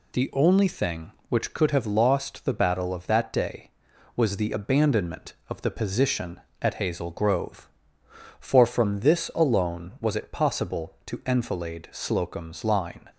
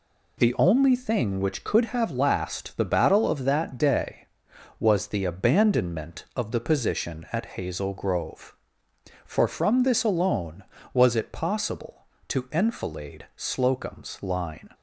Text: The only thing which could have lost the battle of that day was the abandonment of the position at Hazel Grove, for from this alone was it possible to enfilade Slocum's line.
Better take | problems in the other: first | says "last" for "lost"; at 2.1 s

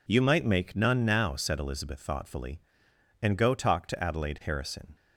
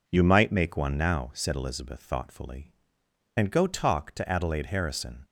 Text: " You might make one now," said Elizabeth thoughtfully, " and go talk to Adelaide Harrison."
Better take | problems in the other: second | says "none" for "one"; at 0.7 s

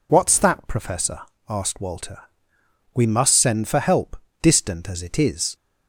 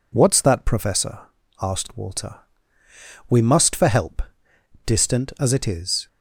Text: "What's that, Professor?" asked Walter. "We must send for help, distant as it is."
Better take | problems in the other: first | skips "send"; at 3.7 s

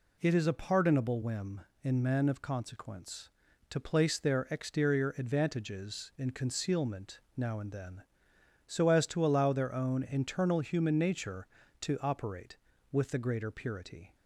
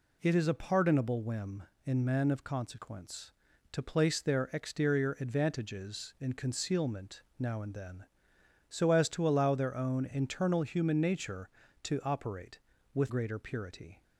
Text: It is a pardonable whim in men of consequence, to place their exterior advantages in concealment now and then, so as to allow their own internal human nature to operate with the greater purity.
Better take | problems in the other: first | pauses between "concealment" and "now"; slight; at 7.2 s; 0.16 s long; slight in the first // skips "the"; at 13.0 s

